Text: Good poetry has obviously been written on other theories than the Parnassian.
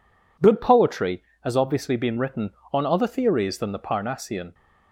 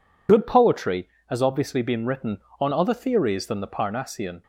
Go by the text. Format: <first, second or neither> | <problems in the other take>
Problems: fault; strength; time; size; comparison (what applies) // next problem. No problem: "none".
first | loses the start of "Good"; at 0.2 s; 40 ms